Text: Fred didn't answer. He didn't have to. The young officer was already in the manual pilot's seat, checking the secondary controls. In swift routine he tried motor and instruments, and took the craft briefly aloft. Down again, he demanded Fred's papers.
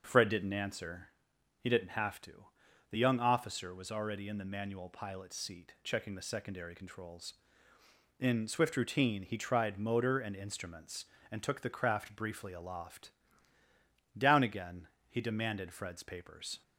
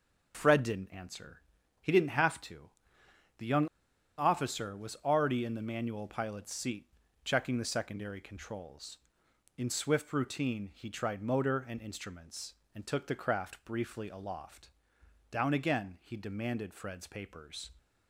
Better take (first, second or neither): first